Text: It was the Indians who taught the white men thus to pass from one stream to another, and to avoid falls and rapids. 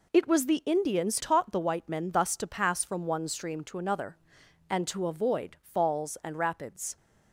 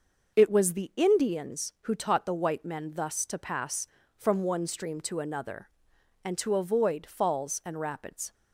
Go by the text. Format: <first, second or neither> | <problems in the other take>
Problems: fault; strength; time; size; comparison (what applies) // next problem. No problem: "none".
second | skips "who"; at 1.1 s